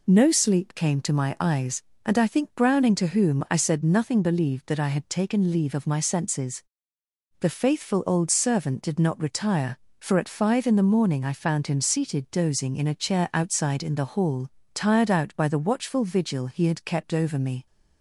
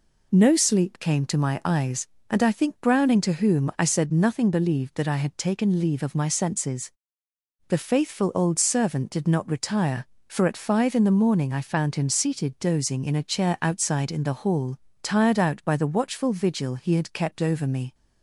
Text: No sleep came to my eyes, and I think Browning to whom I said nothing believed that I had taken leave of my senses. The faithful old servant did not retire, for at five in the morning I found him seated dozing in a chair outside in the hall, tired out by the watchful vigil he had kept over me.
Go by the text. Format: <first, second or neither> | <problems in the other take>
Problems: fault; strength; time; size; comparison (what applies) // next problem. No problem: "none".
neither | none